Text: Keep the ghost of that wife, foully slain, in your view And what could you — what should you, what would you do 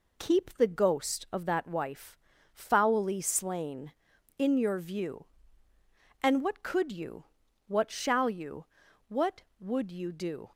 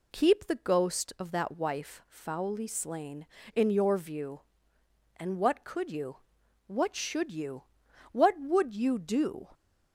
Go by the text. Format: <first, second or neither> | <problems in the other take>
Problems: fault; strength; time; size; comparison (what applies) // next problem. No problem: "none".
second | says "shall" for "should"; at 7.8 s